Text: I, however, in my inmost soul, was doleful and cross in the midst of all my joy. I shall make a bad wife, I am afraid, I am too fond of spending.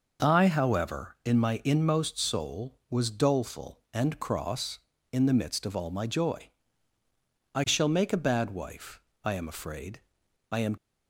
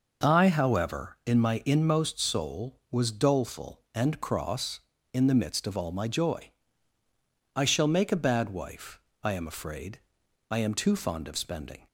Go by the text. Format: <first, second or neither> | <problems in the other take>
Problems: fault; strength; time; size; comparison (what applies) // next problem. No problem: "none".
second | stops before "too fond of spending"; at 10.7 s